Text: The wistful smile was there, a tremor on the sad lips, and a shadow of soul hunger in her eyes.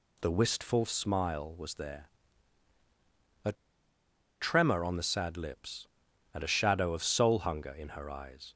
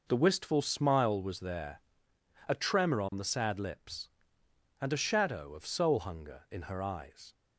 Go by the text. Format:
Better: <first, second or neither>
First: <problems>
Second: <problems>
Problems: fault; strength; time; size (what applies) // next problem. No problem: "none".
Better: second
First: pauses between "a" and "tremor"; noticeable; at 3.5 s; 0.87 s long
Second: none